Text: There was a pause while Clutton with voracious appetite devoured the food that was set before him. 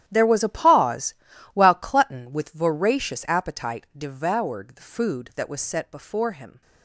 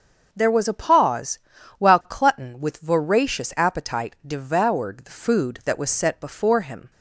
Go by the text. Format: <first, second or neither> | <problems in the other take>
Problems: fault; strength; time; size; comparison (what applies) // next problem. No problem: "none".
second | gets quieter; strong; throughout; 14.5 dB // starts louder than the rest; strong; until 1.0 s; 11.5 dB; also in the second // pauses between "pause" and "while"; at 1.1 s; 0.38 s long; also in the second